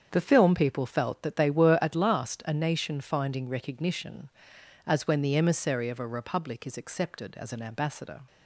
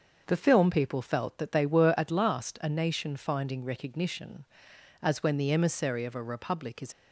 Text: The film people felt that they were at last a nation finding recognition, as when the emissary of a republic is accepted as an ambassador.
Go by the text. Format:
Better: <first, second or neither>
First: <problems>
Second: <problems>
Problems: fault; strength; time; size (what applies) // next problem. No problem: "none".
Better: first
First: starts louder than the rest; strong; until 1.1 s; 7.5 dB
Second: starts louder than the rest; until 1.2 s; 6.5 dB // stops before "accepted as an ambassador"; at 6.9 s